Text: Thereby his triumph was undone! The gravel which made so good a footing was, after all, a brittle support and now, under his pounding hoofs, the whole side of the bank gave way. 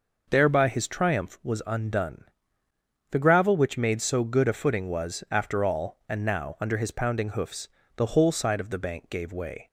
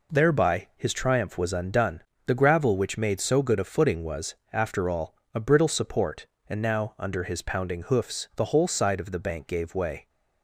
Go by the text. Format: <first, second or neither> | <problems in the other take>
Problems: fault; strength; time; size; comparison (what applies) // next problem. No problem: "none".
second | skips "a brittle support"; at 6.0 s